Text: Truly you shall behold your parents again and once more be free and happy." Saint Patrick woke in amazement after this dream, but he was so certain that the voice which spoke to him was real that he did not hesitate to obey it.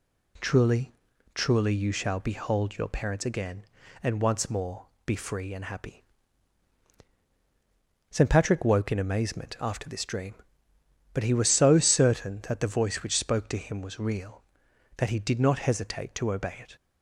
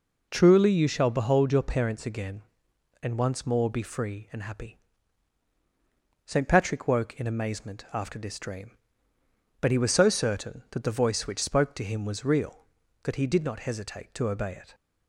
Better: second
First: says "Truly" twice; at 1.3 s // pauses between "more" and "be"; slight; at 4.8 s; 0.18 s long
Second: none

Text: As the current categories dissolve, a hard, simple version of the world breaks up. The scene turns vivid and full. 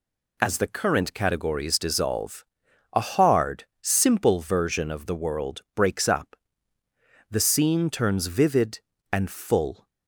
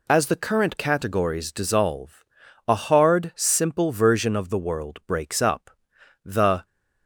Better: first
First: none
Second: stops before "scene turns vivid and full"; at 6.6 s

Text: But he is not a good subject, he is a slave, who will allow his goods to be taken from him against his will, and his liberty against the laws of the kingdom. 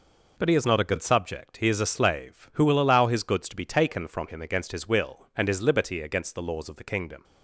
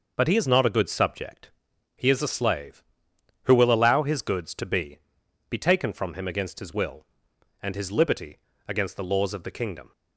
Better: first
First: none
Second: says "be" twice; at 5.4 s // pauses between "liberty" and "against"; slight; at 8.3 s; 0.30 s long

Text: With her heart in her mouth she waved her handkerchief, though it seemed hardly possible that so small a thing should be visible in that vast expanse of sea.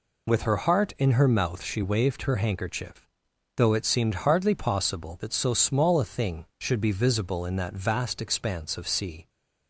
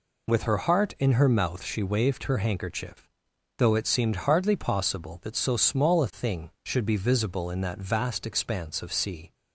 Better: neither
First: none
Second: none

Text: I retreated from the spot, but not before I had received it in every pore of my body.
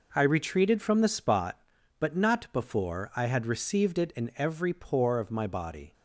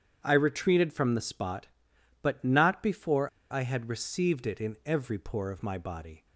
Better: first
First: none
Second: starts louder than the rest; strong; until 1.2 s; 8 dB // pauses between "before" and "I"; slight; at 3.2 s; 0.22 s long

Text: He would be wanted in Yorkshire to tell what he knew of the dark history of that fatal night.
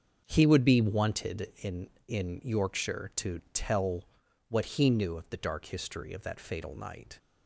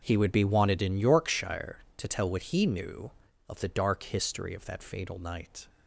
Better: second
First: starts louder than the rest; until 1.2 s; 7 dB // says "in" twice; at 2.0 s // pauses between "tell" and "what"; at 4.0 s; 0.44 s long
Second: starts louder than the rest; noticeable; until 1.0 s; 6 dB

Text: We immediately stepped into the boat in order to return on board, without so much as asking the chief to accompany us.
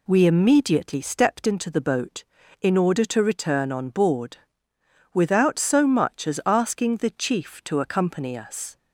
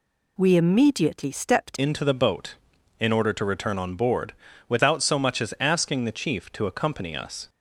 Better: first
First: none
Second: changes voice at "into"; from 1.7 s on; 5.7 s long

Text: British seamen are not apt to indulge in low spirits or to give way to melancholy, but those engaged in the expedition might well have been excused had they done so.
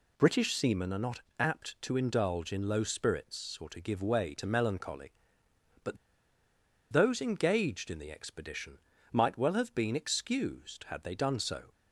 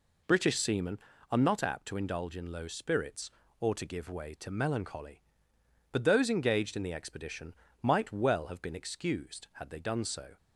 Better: second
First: pauses between "not" and "apt"; slight; at 1.1 s; 0.20 s long // pauses between "but" and "those"; noticeable; at 5.9 s; 0.96 s long // pauses between "expedition" and "might"; slight; at 8.7 s; 0.34 s long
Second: pauses between "expedition" and "might"; slight; at 7.5 s; 0.26 s long

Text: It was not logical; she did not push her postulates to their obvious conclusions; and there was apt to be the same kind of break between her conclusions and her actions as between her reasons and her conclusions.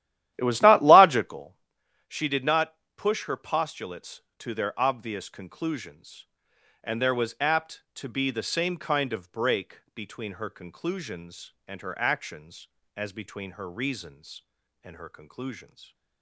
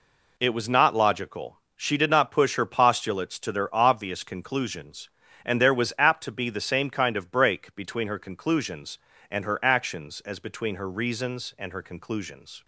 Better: second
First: starts louder than the rest; strong; until 1.6 s; 13 dB // pauses between "not" and "push"; slight; at 2.7 s; 0.20 s long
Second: none

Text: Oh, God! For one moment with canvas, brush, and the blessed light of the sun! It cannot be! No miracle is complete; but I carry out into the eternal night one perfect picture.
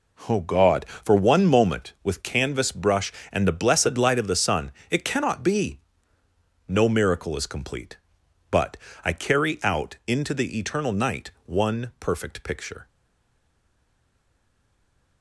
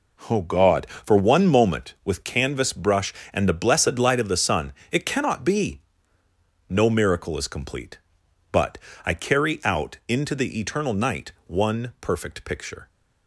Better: second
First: pauses between "but" and "I"; slight; at 8.7 s; 0.26 s long // pauses between "night" and "one"; slight; at 11.3 s; 0.16 s long // stays silent after the last word; from 12.8 s on; 2.4 s long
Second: pauses between "but" and "I"; slight; at 8.7 s; 0.26 s long // pauses between "night" and "one"; slight; at 11.3 s; 0.16 s long

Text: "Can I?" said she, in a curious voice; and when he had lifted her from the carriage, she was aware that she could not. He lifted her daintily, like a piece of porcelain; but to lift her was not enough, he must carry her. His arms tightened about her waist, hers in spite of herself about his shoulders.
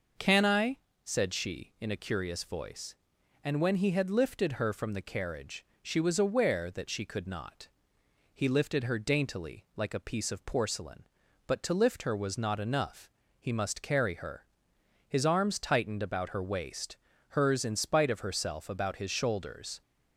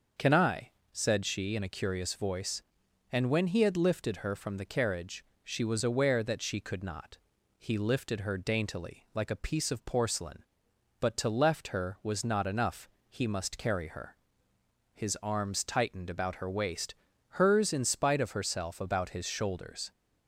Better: first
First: none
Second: starts louder than the rest; until 1.4 s; 6.5 dB // says "left" for "lift"; at 11.2 s

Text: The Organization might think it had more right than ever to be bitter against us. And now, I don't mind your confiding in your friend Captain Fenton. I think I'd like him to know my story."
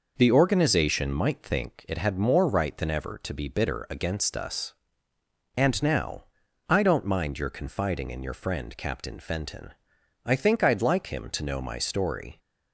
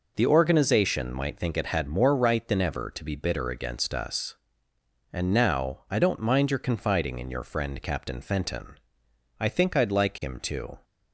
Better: first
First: none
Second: stops before "know my story"; at 10.8 s

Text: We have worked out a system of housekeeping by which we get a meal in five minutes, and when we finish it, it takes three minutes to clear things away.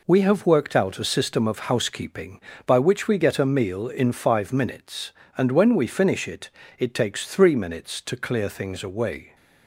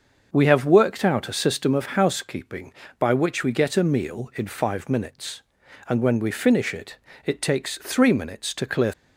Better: first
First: none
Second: starts louder than the rest; until 1.3 s; 6 dB // stops before "things away"; at 8.9 s

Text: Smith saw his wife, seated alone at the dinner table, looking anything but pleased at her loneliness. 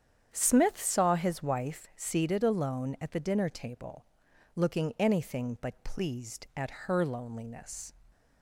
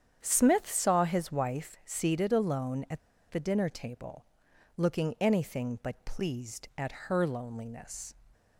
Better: first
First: starts louder than the rest; strong; until 1.3 s; 8.5 dB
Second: starts louder than the rest; strong; until 1.2 s; 8.5 dB // pauses between "at" and "the"; slight; at 2.9 s; 0.31 s long

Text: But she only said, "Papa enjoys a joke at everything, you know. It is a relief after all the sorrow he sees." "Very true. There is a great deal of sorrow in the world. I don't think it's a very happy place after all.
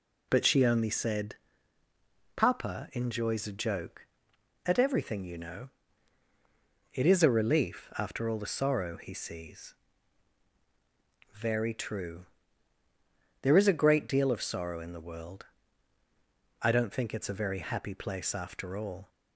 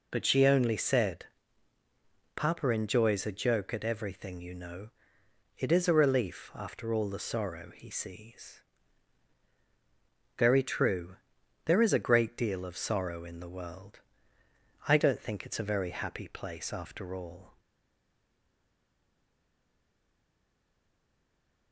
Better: first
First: none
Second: stays silent after the last word; strong; from 17.5 s on; 4.2 s long

